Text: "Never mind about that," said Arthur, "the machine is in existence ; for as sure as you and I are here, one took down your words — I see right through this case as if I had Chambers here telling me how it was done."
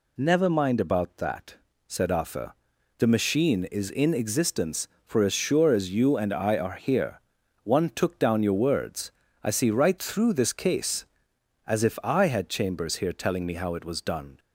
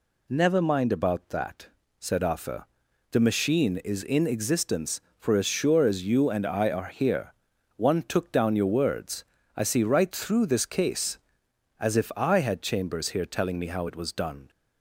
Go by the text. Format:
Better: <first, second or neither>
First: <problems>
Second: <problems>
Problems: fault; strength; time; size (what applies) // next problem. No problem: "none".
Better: neither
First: none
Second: none